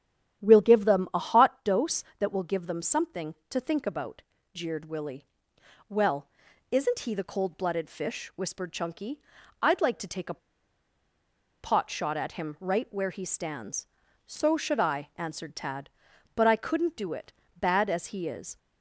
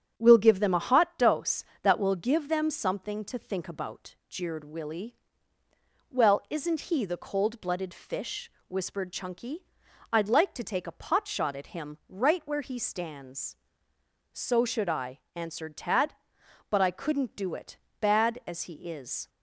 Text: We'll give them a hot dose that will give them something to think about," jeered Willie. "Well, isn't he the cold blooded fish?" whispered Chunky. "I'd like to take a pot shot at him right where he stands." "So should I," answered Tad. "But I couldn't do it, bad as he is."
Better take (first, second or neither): second